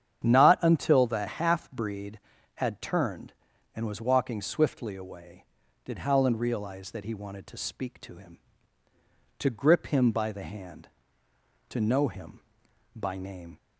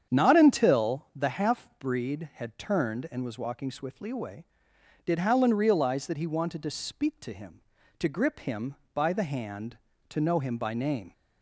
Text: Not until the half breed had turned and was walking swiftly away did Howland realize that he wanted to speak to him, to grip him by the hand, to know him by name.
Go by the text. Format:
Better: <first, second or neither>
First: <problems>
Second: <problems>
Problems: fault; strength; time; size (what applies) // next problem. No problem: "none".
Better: neither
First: starts louder than the rest; strong; until 1.2 s; 8.5 dB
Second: starts louder than the rest; strong; until 1.2 s; 8 dB